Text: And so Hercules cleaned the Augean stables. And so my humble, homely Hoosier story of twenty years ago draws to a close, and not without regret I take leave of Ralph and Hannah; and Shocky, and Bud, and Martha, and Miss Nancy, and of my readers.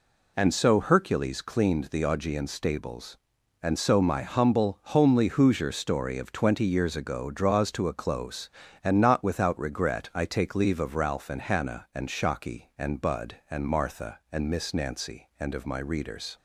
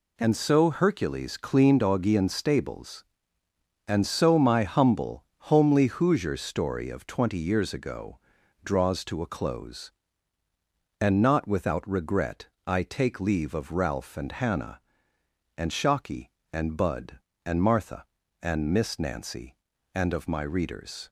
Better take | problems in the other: first | skips "the"; at 1.8 s // pauses between "ago" and "draws"; at 8.1 s; 0.44 s long // pauses between "regret" and "I"; slight; at 12.4 s; 0.18 s long

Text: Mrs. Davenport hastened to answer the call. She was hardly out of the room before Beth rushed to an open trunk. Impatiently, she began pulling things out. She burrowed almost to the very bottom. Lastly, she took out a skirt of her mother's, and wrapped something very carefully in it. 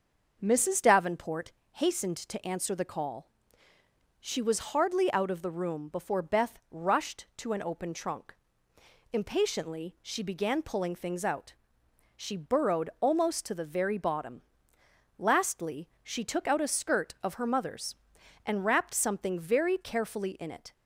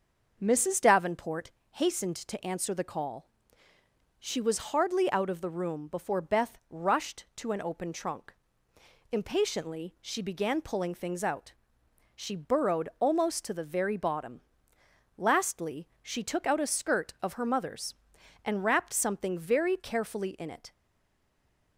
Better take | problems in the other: first | starts louder than the rest; until 1.4 s; 6.5 dB; also in the first // pauses between "Davenport" and "hastened"; slight; at 1.4 s; 0.22 s long; slight in the first // stays silent after the last word; from 20.7 s on; 1.0 s long

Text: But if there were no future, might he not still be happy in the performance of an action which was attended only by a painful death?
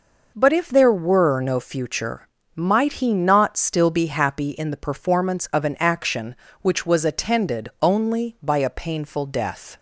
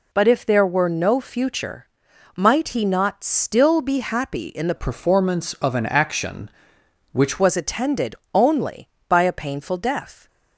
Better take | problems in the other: first | changes voice from "performance" to "which"; from 4.7 to 7.3 s; 2.6 s long // pauses between "attended" and "only"; slight; at 8.1 s; 0.18 s long

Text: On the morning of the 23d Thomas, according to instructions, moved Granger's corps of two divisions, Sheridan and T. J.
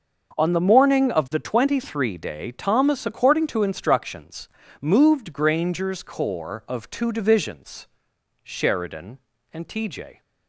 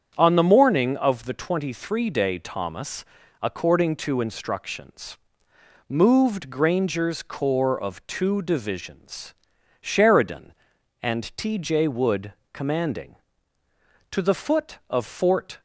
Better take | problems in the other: first | starts louder than the rest; strong; until 1.1 s; 8 dB; also in the first // goes on to say "Wood commanding to the foot of Fort"; strong; from 11.8 s on; 3.7 s long

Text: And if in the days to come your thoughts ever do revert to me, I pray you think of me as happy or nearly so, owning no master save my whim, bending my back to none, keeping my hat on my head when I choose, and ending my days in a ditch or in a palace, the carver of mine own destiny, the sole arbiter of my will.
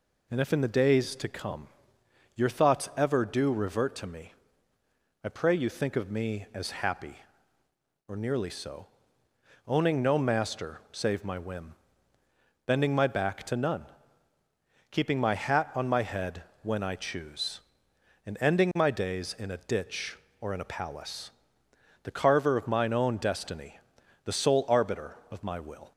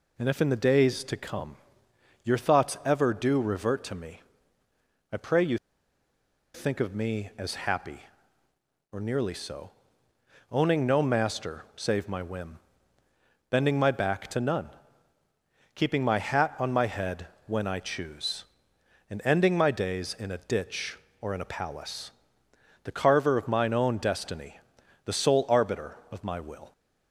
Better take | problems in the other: first | pauses between "come" and "your"; noticeable; at 1.5 s; 0.68 s long; noticeable in the first // pauses between "you" and "think"; noticeable; at 5.5 s; 0.98 s long // pauses between "head" and "when"; slight; at 17.2 s; 0.18 s long; slight in the first

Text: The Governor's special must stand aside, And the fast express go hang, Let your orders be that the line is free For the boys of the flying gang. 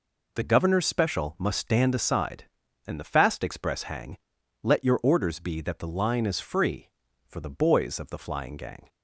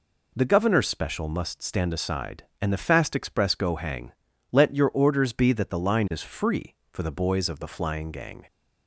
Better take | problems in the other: second | skips "go"; at 3.8 s

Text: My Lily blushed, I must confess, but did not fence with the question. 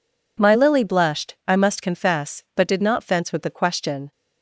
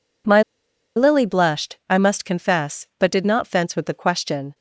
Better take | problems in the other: first | pauses between "My" and "Lily"; noticeable; at 0.4 s; 0.54 s long

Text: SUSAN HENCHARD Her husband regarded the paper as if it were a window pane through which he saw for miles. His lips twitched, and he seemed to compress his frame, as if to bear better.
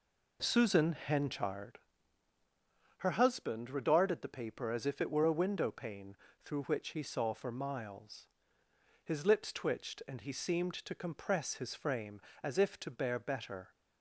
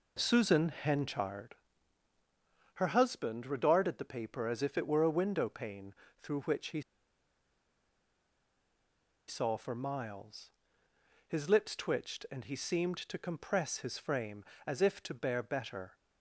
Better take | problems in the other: first | pauses between "HENCHARD" and "Her"; at 1.5 s; 1.2 s long; also in the first // pauses between "pane" and "through"; slight; at 5.9 s; 0.30 s long; slight in the first // pauses between "he" and "saw"; strong; at 6.8 s; 2.4 s long

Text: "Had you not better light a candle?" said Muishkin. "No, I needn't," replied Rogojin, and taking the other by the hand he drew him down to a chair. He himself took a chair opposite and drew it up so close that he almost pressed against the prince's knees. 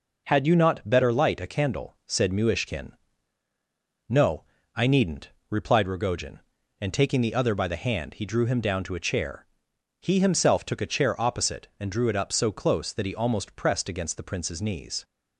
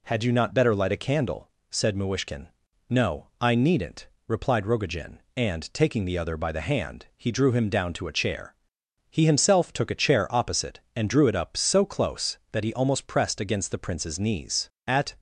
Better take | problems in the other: first | goes on to say "At"; slight; from 14.8 s on; 0.28 s long

